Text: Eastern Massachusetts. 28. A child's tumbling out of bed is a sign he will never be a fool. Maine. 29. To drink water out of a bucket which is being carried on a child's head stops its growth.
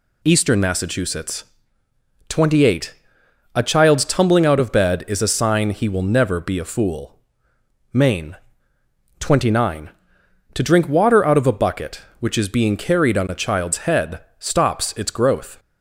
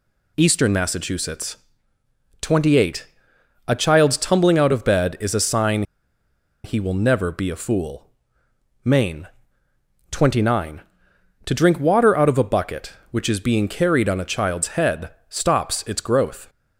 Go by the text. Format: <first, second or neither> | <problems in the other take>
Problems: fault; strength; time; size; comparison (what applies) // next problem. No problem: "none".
first | pauses between "sign" and "he"; noticeable; at 5.8 s; 0.81 s long // pauses between "head" and "stops"; slight; at 15.1 s; 0.18 s long; slight in the first